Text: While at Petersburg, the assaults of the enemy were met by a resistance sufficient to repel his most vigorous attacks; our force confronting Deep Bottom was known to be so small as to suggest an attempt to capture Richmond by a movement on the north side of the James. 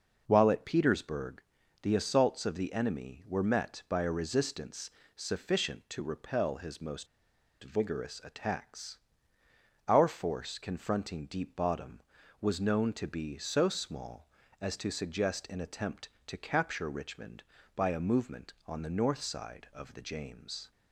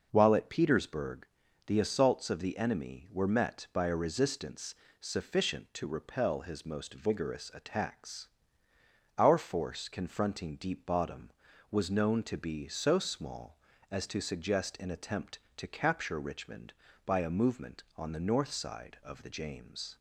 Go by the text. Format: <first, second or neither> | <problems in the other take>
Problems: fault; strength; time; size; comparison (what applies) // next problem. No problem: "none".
second | pauses between "resistance" and "sufficient"; slight; at 4.9 s; 0.24 s long; slight in the second // pauses between "most" and "vigorous"; noticeable; at 7.0 s; 0.56 s long